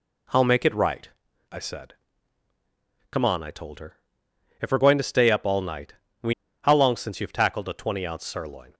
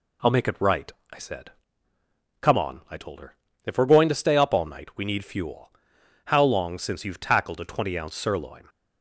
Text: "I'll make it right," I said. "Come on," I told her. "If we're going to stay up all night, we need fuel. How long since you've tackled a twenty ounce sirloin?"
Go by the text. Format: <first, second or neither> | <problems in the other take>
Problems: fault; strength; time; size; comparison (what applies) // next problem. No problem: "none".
second | skips "need fuel"; at 6.4 s